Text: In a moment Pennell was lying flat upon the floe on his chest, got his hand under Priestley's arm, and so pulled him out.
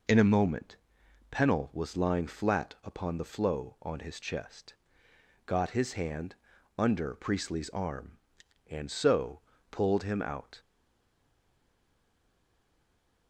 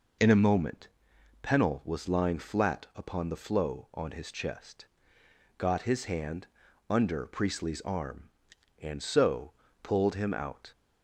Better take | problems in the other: second | pauses between "moment" and "Pennell"; noticeable; at 0.7 s; 0.54 s long; noticeable in the second // pauses between "hand" and "under"; at 6.3 s; 0.44 s long; also in the second // pauses between "so" and "pulled"; slight; at 9.4 s; 0.28 s long; slight in the second // stays silent after the last word; strong; from 10.5 s on; 2.7 s long

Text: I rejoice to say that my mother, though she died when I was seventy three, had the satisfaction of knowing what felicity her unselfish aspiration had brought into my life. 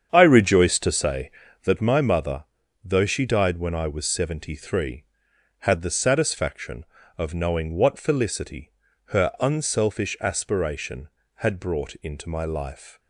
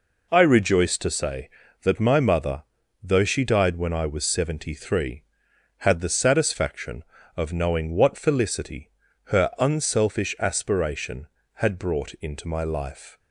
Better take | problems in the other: second | starts louder than the rest; strong; until 1.8 s; 8 dB // pauses between "felicity" and "her"; slight; at 8.7 s; 0.36 s long; slight in the second

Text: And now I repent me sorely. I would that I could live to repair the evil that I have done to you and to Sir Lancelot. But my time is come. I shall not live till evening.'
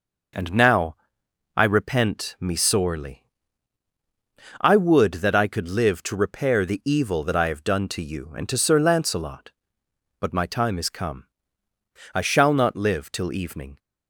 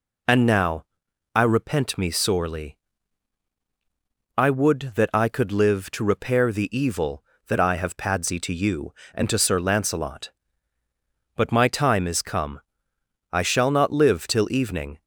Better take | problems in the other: first | pauses between "now" and "I"; noticeable; at 0.8 s; 0.50 s long; noticeable in the first // says "padsy" for "done"; at 7.9 s

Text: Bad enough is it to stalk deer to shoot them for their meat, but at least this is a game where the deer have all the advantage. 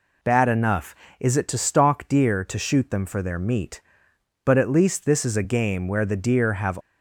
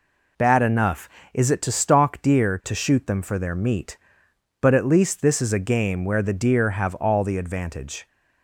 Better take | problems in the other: second | stops before "all the advantage"; at 6.8 s

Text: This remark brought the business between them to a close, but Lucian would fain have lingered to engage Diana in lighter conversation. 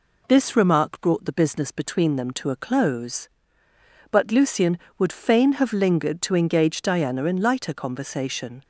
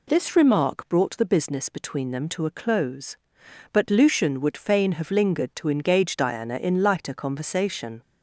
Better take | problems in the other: neither | none

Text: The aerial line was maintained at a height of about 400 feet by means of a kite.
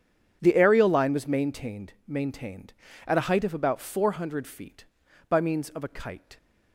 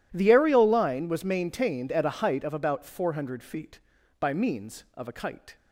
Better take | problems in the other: second | starts louder than the rest; strong; until 1.4 s; 8.5 dB // says "maintained" twice; at 2.0 s

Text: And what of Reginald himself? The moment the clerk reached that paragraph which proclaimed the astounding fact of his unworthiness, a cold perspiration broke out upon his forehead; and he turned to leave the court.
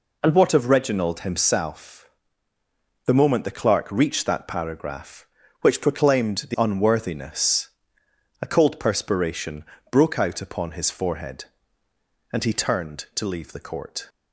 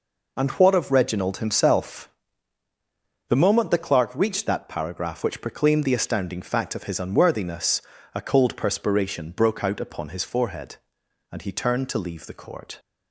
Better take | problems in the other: second | skips "astounding fact of his"; at 6.5 s // pauses between "perspiration" and "broke"; slight; at 9.6 s; 0.28 s long

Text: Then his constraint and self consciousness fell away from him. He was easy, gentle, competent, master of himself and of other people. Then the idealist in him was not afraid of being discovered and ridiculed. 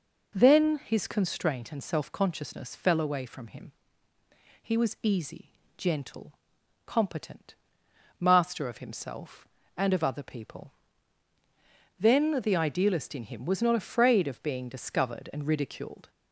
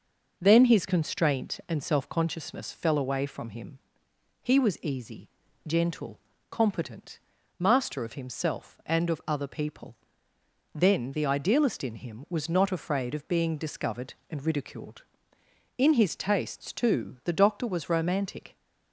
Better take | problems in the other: first | goes on to say "In his tastes too the doctor was romantic"; strong; from 15.7 s on; 2.7 s long

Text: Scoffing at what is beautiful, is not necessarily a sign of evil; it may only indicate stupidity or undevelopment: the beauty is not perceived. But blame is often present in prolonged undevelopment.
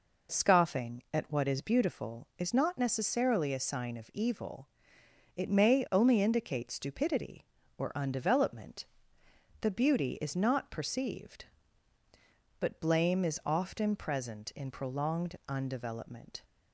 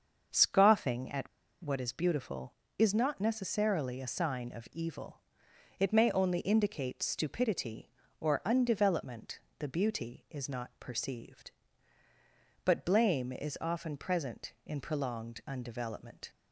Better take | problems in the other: first | starts louder than the rest; until 1.6 s; 6.5 dB // pauses between "at" and "what"; slight; at 1.2 s; 0.33 s long

